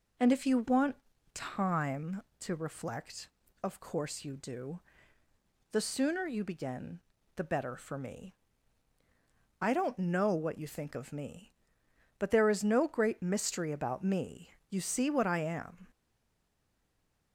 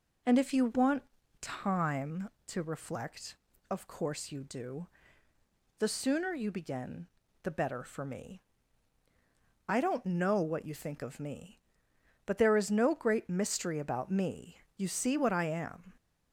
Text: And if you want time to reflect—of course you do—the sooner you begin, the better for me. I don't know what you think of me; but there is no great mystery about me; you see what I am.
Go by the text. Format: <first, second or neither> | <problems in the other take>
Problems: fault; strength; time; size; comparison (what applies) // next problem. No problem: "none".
second | pauses between "want" and "time"; at 0.9 s; 0.38 s long; also in the second // stays silent after the last word; noticeable; from 15.9 s on; 1.4 s long